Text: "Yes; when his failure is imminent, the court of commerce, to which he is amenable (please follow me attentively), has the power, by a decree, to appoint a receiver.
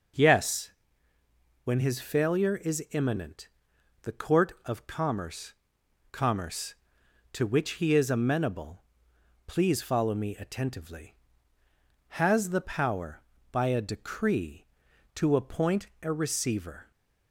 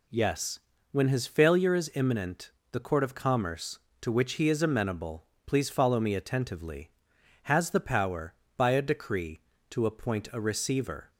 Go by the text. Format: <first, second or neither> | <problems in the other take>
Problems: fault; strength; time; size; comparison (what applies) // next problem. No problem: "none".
second | says "commerce" twice; at 6.1 s // pauses between "appoint" and "a"; slight; at 15.8 s; 0.16 s long